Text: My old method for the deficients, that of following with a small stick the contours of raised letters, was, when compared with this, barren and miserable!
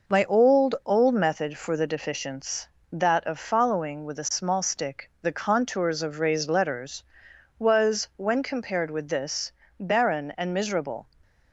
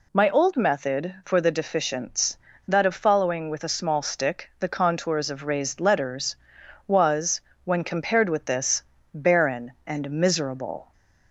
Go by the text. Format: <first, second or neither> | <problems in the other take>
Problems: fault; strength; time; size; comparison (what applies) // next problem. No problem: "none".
second | says "old" twice; at 0.8 s